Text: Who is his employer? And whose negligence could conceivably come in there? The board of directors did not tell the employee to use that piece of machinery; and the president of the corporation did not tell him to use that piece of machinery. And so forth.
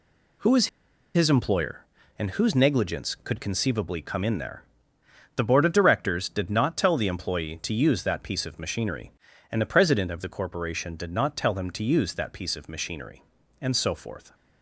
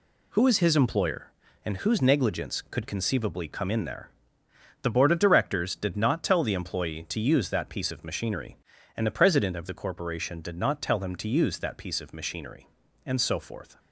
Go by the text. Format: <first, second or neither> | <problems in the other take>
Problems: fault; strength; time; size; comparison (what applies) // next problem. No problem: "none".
second | pauses between "is" and "his"; noticeable; at 0.6 s; 0.47 s long